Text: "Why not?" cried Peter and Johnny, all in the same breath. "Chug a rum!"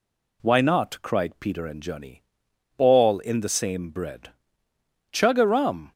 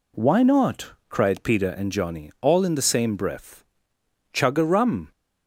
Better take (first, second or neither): second